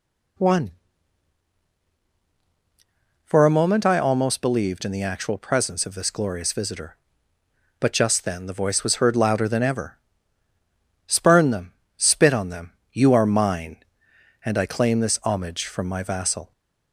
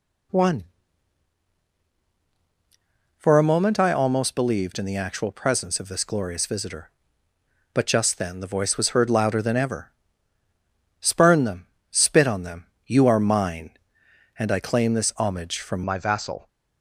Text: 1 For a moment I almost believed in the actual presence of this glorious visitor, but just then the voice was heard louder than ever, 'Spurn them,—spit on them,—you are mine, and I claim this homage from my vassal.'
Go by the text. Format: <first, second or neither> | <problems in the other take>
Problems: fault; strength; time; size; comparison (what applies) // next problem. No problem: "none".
first | changes voice at "my"; from 15.8 s on; 0.6 s long